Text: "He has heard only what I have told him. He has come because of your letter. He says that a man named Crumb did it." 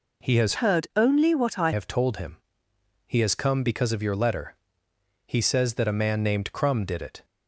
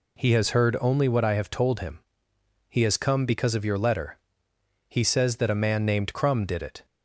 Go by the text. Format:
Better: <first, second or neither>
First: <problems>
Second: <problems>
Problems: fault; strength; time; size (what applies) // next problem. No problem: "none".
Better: second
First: changes voice from "heard" to "I"; from 0.5 to 1.7 s; 1.2 s long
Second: none